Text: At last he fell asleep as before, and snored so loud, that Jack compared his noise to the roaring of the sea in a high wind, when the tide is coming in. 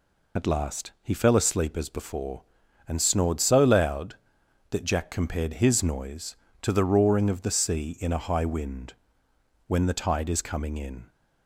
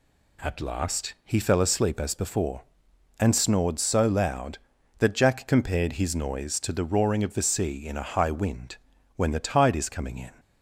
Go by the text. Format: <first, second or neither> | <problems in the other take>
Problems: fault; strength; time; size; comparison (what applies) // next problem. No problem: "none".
second | loses the start of "At"; at 0.3 s; 75 ms